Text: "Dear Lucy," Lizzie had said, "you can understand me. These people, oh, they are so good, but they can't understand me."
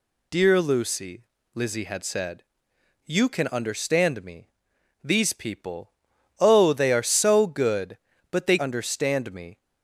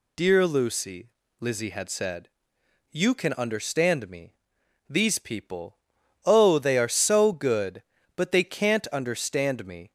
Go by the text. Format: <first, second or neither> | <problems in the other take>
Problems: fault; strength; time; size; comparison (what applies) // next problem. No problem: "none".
second | skips "can't"; at 8.5 s